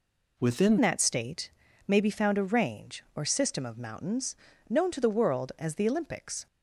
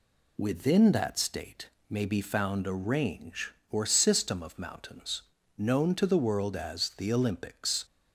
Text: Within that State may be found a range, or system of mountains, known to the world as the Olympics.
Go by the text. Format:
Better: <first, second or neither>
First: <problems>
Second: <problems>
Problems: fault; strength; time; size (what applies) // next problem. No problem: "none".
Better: second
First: changes voice at "that"; from 0.8 s on; 5.6 s long // pauses between "State" and "may"; at 1.4 s; 0.40 s long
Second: pauses between "State" and "may"; slight; at 1.6 s; 0.18 s long